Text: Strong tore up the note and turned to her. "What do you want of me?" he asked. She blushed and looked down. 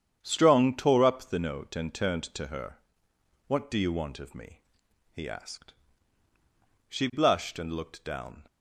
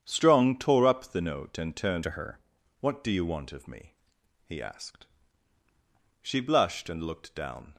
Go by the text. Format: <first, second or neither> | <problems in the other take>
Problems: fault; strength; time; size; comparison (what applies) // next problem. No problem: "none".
first | starts louder than the rest; strong; until 1.0 s; 8.5 dB; strong in the first // changes voice from "to" to "her"; from 2.0 to 2.3 s; 0.3 s long